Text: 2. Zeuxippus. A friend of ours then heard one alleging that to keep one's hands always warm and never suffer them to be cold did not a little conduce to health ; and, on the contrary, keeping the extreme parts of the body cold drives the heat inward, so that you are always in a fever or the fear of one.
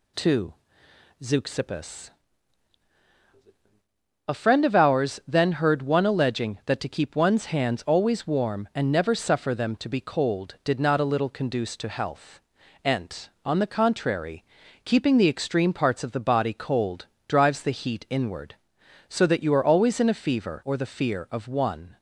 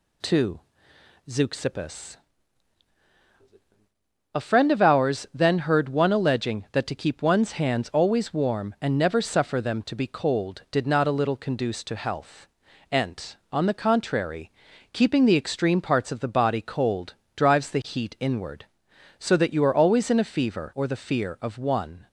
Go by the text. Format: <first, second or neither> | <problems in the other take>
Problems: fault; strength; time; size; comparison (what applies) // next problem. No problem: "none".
neither | pauses between "cold" and "drives"; slight; the same in both